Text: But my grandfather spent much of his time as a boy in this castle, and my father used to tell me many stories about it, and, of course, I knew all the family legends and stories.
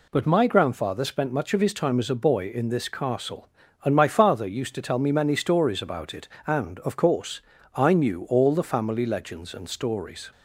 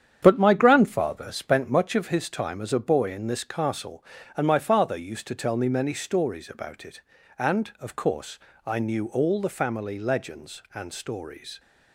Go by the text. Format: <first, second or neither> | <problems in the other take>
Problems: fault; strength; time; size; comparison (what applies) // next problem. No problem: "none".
first | starts louder than the rest; strong; until 1.7 s; 9 dB